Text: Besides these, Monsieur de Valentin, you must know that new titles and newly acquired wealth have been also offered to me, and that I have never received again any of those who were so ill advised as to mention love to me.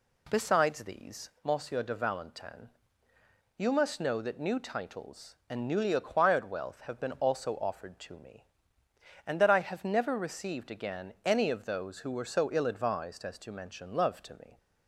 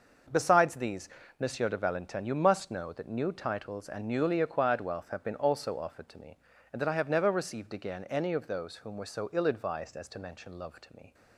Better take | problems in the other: first | starts louder than the rest; until 1.6 s; 6 dB // says "whom" for "who"; at 8.7 s

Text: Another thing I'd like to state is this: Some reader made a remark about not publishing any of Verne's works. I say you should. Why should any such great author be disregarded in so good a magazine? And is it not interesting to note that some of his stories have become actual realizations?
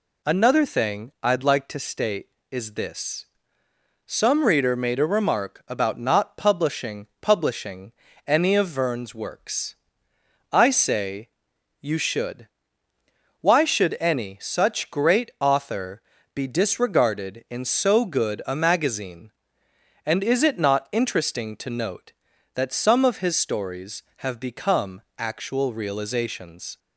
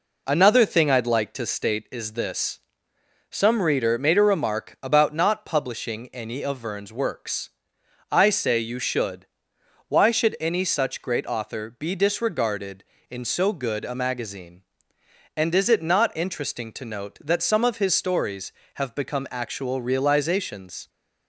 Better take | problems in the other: second | says "publishing" twice; at 7.2 s // pauses between "say" and "you"; noticeable; at 11.2 s; 0.52 s long // pauses between "author" and "be"; slight; at 16.0 s; 0.34 s long // pauses between "become" and "actual"; slight; at 25.0 s; 0.16 s long

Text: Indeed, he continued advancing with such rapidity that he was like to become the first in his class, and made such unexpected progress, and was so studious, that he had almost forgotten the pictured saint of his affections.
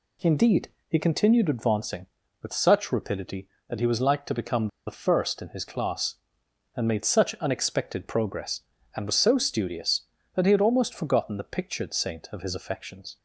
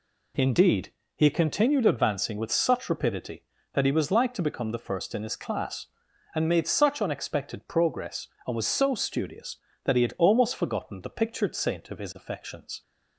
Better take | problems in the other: second | pauses between "become" and "the"; slight; at 4.6 s; 0.18 s long

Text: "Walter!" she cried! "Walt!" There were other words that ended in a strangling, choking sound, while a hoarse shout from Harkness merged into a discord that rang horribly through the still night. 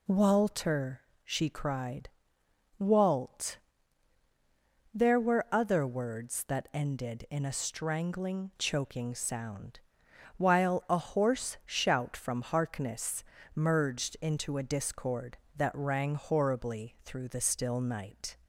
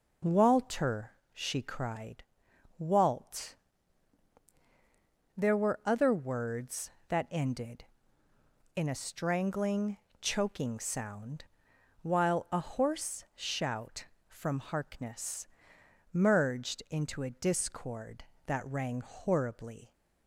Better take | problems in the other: first | pauses between "Harkness" and "merged"; noticeable; at 15.4 s; 0.64 s long; slight in the first // stops before "through the still night"; at 19.9 s

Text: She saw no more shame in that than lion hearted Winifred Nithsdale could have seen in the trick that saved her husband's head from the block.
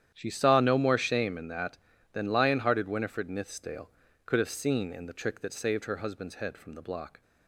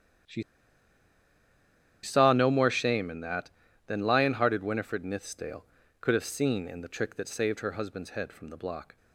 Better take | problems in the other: first | starts louder than the rest; strong; until 2.8 s; 10 dB; strong in the first // pauses between "She" and "saw"; strong; at 0.4 s; 1.6 s long

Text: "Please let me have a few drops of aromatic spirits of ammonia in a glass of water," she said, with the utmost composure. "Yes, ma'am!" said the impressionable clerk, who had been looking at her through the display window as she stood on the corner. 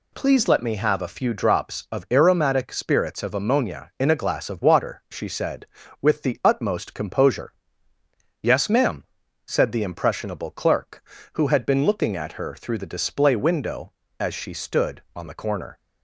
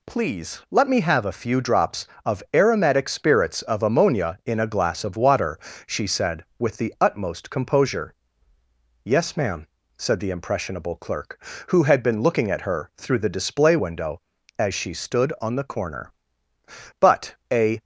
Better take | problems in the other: first | goes on to say "But a"; noticeable; from 16.9 s on; 0.80 s long

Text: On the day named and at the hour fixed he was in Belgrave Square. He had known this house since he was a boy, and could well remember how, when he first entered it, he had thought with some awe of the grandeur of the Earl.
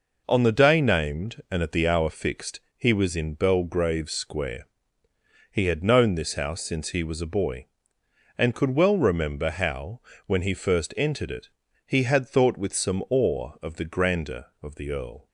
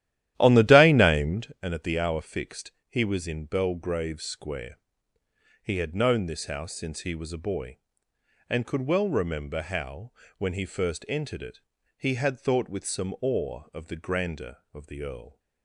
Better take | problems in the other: first | starts louder than the rest; strong; until 1.6 s; 13 dB // pauses between "fixed" and "he"; slight; at 2.7 s; 0.16 s long; slight in the first

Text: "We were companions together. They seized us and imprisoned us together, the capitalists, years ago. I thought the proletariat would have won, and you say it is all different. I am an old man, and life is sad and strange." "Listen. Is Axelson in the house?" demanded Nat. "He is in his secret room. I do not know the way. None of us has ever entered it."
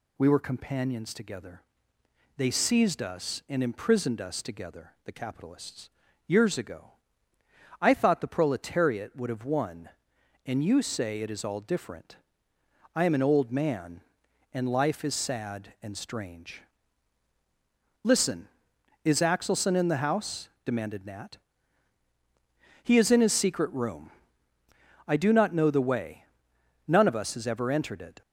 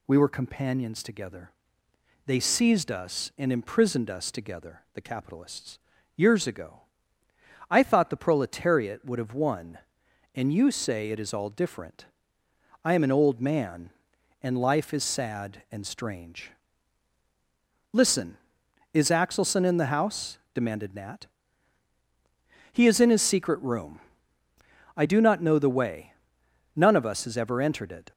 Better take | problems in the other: neither | none

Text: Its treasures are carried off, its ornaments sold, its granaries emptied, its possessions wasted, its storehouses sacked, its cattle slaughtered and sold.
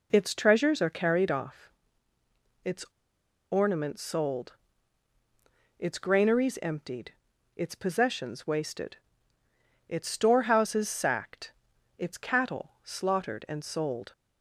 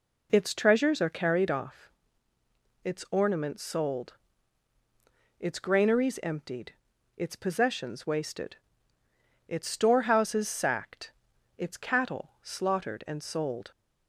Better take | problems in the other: second | pauses between "its" and "ornaments"; noticeable; at 2.8 s; 0.68 s long

